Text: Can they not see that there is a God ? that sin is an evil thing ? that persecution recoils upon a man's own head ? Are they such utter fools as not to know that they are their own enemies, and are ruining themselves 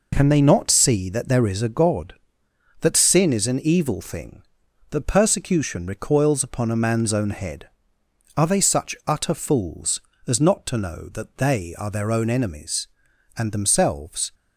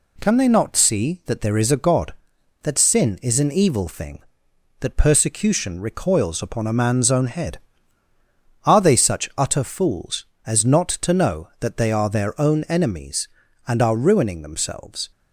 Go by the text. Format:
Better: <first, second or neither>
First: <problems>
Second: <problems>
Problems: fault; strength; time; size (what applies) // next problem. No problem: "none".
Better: second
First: skips "are ruining"; at 13.5 s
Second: none